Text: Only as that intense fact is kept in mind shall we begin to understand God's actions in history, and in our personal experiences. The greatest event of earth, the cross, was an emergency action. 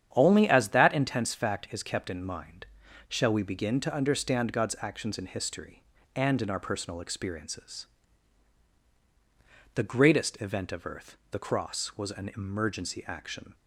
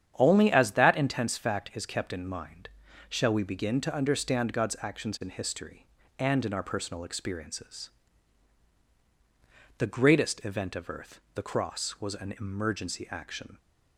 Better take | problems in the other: neither | starts louder than the rest; strong; the same in both // pauses between "mind" and "shall"; the same in both

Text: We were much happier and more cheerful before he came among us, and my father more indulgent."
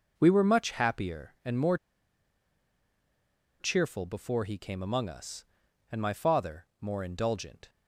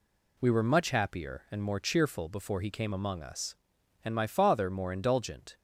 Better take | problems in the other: second | pauses between "more" and "cheerful"; strong; at 1.7 s; 1.8 s long

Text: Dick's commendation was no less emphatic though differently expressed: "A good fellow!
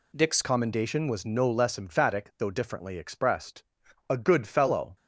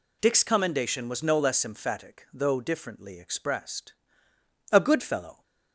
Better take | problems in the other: second | changes voice at "commendation"; from 0.4 s on; 4.5 s long

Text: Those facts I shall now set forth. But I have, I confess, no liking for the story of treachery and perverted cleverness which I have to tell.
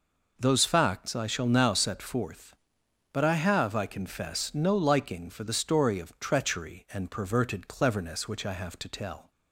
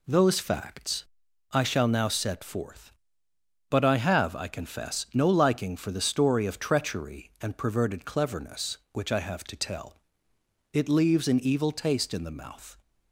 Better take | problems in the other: first | pauses between "facts" and "I"; noticeable; at 1.0 s; 0.46 s long // goes on to say "It leaves an evil taste in the mouth"; strong; from 10.7 s on; 2.0 s long

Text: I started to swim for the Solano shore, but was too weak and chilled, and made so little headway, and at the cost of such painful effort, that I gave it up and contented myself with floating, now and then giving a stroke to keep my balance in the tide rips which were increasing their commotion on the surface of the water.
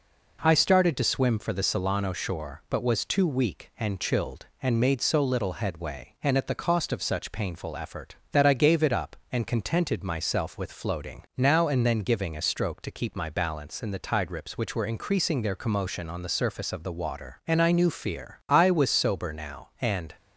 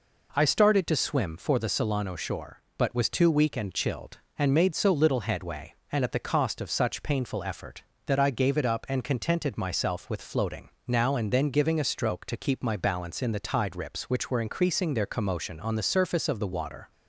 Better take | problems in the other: second | goes on to say "And I knew fear I was sober now and"; strong; from 17.4 s on; 2.6 s long

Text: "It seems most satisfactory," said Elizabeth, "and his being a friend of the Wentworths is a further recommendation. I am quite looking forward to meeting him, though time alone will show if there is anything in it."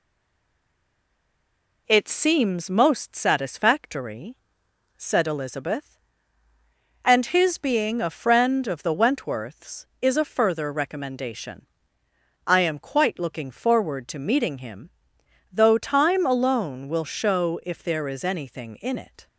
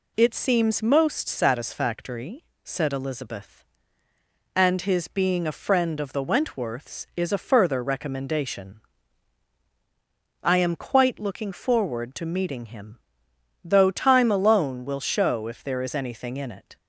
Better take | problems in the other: second | stays silent before the first word; noticeable; until 1.8 s; 1.8 s long

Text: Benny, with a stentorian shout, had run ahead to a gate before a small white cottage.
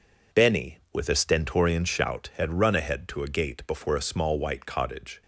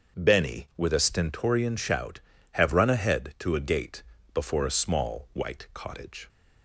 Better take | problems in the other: first | starts louder than the rest; until 1.2 s; 6.5 dB // says "have" for "had"; at 2.5 s // pauses between "gate" and "before"; slight; at 4.0 s; 0.30 s long

